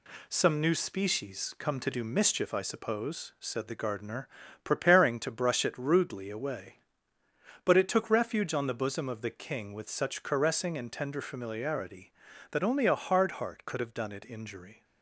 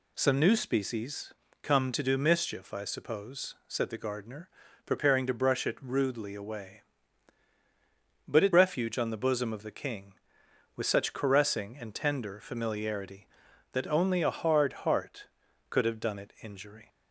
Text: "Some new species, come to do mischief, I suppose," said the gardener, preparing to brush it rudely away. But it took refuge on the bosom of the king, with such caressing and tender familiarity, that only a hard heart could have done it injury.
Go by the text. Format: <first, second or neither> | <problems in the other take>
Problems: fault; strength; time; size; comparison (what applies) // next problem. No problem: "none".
first | skips "took"; at 8.5 s